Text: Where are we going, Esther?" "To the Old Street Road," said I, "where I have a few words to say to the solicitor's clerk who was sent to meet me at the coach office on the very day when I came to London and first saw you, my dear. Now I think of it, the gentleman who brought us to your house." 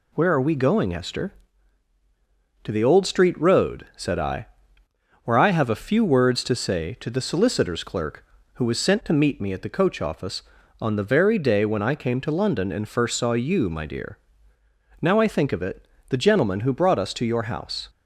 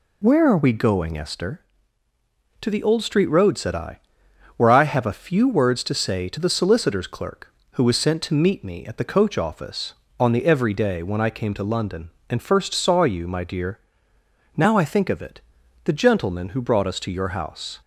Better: first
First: none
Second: says "every" for "very"; at 10.4 s

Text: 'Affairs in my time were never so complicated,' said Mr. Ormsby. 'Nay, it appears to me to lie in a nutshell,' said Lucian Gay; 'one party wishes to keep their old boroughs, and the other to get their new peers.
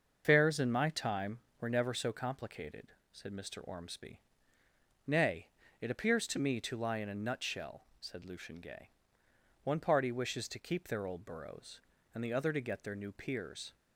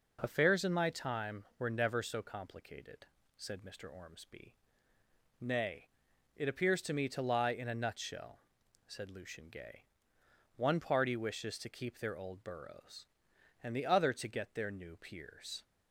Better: second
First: loses the start of "Affairs"; at 0.2 s; 145 ms // starts louder than the rest; until 1.2 s; 6.5 dB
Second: none

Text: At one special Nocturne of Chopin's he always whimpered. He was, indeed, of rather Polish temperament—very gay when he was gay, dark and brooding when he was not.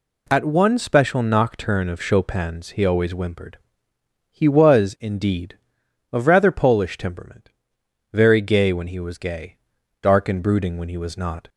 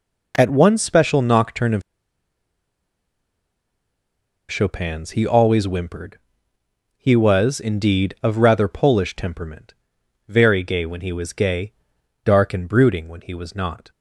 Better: first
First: none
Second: pauses between "of" and "Chopin's"; strong; at 1.8 s; 2.6 s long

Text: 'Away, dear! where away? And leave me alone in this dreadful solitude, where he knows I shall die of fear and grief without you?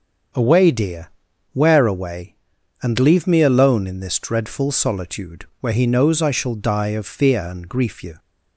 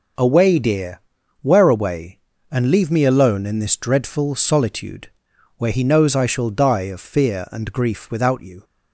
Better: second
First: starts louder than the rest; until 1.8 s; 7 dB // skips "without"; at 8.0 s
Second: none

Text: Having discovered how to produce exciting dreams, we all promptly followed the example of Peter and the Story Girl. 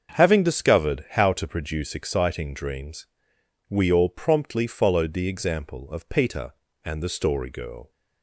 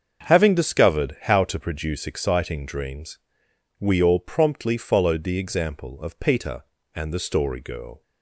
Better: neither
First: starts louder than the rest; until 1.1 s; 7 dB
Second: starts louder than the rest; until 1.3 s; 7 dB

